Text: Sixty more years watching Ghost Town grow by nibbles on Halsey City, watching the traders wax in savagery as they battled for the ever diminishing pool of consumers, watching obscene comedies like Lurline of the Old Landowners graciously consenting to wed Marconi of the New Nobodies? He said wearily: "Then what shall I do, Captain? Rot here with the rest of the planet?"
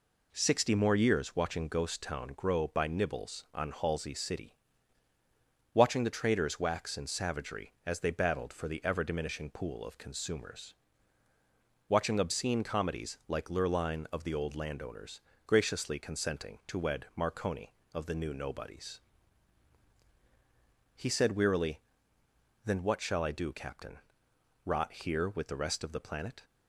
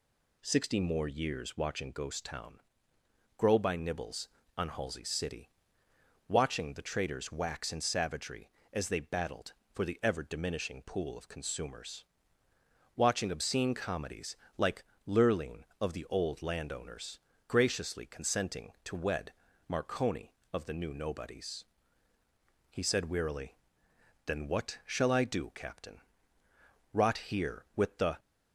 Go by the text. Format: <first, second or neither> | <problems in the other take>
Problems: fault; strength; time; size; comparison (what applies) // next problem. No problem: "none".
first | pauses between "Town" and "grow"; noticeable; at 2.6 s; 0.76 s long // pauses between "comedies" and "like"; slight; at 14.3 s; 0.20 s long // pauses between "like" and "Lurline"; slight; at 14.8 s; 0.20 s long // pauses between "Landowners" and "graciously"; slight; at 17.1 s; 0.30 s long; slight in the first // pauses between "wed" and "Marconi"; slight; at 19.3 s; 0.34 s long // stops before "rest of the planet"; at 28.1 s